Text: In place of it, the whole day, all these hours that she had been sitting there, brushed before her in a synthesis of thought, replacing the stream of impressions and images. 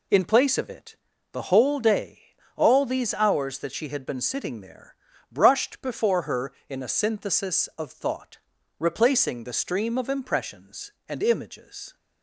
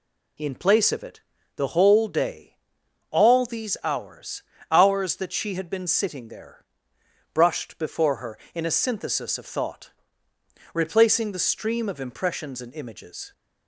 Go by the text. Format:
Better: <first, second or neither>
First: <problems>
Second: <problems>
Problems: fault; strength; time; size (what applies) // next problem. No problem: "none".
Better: first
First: none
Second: says "hours" twice; at 4.7 s